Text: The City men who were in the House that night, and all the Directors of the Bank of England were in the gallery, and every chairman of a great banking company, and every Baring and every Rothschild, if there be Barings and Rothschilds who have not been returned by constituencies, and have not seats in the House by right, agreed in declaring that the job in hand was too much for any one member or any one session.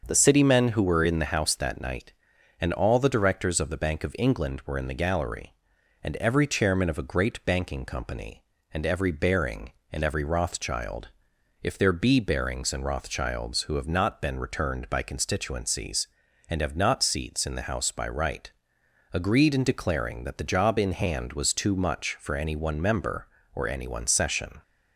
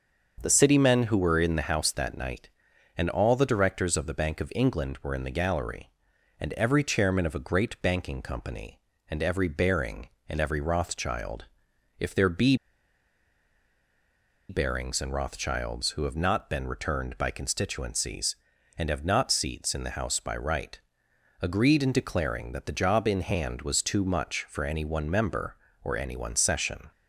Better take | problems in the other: first | starts louder than the rest; until 1.4 s; 6.5 dB; also in the first // pauses between "be" and "Barings"; strong; at 12.5 s; 1.9 s long

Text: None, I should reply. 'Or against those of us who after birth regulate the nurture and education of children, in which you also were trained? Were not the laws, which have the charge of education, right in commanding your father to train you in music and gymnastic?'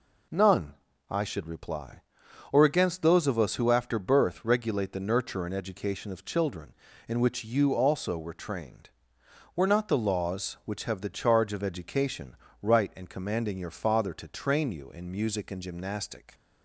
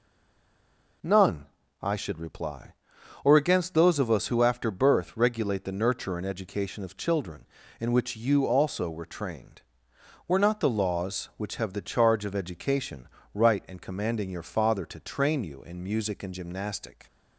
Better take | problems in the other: first | stays silent before the first word; until 1.0 s; 1.0 s long

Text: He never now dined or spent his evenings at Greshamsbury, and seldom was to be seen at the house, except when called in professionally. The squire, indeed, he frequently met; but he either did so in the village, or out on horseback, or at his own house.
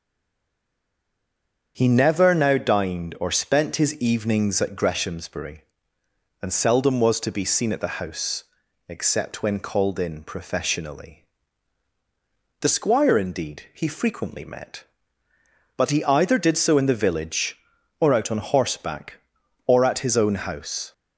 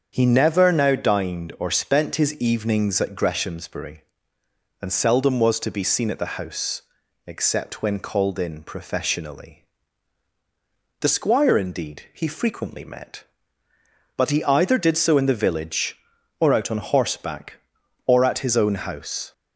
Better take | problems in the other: second | stays silent before the first word; noticeable; until 1.7 s; 1.7 s long // starts louder than the rest; until 2.7 s; 7 dB; also in the second

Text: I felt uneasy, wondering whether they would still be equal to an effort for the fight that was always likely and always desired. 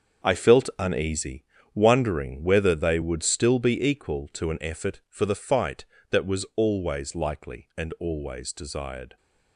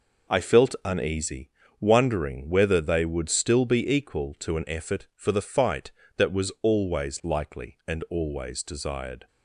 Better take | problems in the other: second | gets quieter; strong; throughout; 11.5 dB

